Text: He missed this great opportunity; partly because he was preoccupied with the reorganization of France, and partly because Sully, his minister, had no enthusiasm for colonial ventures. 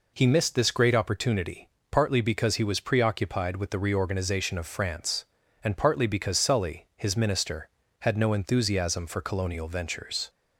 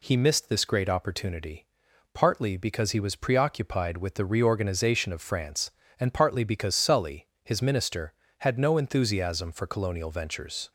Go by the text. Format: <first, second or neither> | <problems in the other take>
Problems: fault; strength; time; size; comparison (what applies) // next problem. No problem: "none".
neither | none